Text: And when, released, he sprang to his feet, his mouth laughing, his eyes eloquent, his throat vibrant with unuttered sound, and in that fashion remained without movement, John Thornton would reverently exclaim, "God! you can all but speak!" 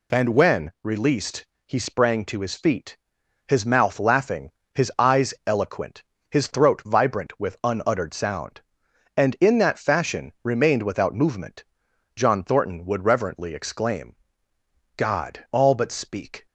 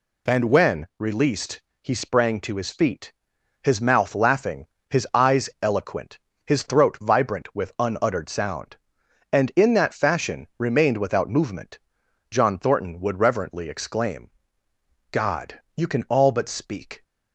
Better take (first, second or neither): second